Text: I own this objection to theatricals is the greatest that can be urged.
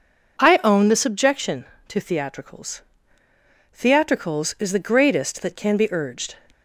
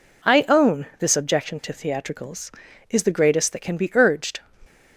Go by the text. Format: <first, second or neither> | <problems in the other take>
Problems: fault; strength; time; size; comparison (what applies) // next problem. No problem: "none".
second | says "theatricals" twice; at 3.7 s